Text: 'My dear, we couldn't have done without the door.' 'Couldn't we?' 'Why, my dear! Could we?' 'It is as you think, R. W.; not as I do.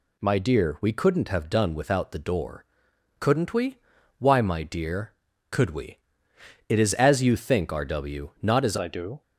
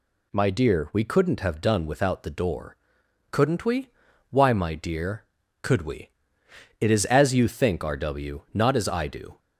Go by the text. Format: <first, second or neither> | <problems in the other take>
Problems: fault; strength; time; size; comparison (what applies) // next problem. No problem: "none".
second | changes voice at "I"; from 8.7 s on; 0.5 s long